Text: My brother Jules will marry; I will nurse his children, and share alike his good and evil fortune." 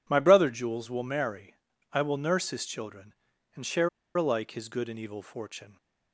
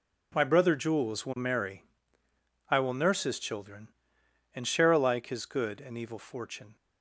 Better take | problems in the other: second | pauses between "share" and "alike"; slight; at 3.8 s; 0.26 s long

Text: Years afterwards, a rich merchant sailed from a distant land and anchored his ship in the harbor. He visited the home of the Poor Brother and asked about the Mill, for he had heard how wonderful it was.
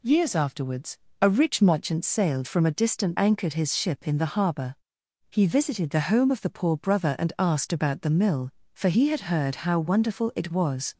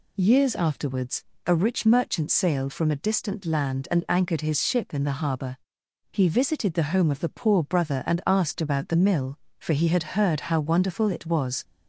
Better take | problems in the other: second | skips "land and"; at 3.1 s

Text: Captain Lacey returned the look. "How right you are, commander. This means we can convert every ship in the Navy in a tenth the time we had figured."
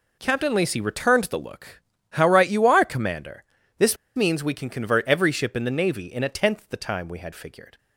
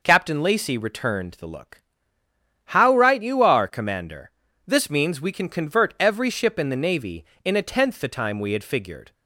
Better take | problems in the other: second | pauses between "This" and "means"; slight; at 3.9 s; 0.19 s long

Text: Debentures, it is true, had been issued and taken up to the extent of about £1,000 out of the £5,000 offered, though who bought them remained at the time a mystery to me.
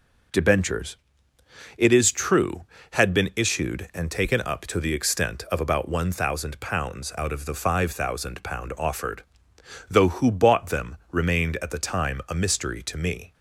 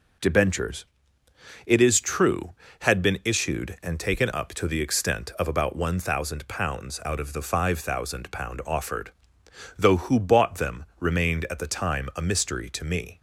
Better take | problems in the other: neither | none

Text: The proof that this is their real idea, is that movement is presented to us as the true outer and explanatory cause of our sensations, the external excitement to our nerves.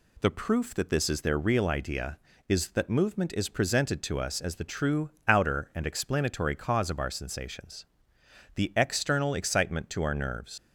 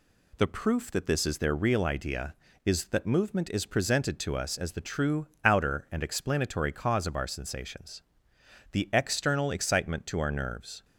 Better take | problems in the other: second | pauses between "true" and "outer"; slight; at 5.0 s; 0.18 s long; slight in the second // leaves "nerves" unfinished; at 10.5 s; 100 ms

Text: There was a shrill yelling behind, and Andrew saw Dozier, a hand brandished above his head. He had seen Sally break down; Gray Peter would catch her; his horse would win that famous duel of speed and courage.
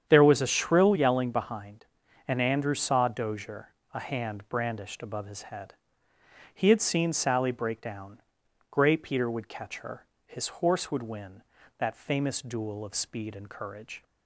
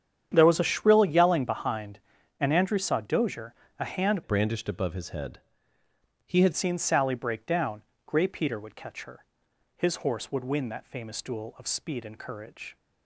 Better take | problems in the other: first | starts louder than the rest; strong; until 1.3 s; 9 dB; strong in the first // changes voice from "brandished" to "had"; from 4.2 to 6.5 s; 2.3 s long

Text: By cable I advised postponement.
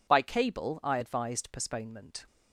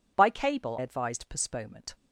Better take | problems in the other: first | skips "I"; at 0.7 s

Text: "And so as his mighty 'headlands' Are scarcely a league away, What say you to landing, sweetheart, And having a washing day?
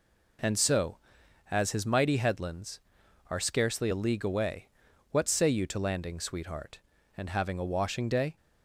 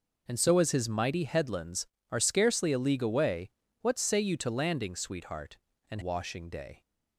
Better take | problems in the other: first | skips "having a"; at 5.9 s

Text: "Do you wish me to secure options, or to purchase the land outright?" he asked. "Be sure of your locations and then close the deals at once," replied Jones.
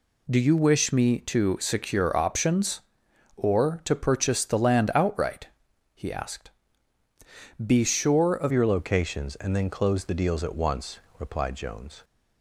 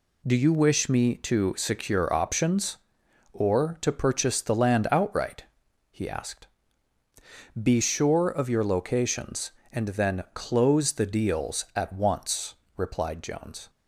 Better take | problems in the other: second | changes voice at "your"; from 8.5 s on; 3.5 s long

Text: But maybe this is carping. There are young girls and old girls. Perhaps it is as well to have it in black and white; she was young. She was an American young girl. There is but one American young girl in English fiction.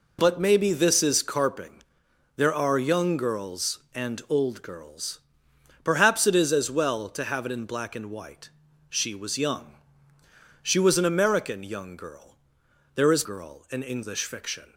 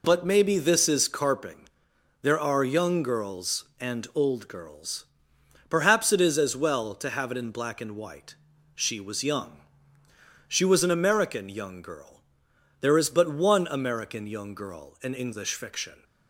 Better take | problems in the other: second | skips "but one American young"; at 13.2 s

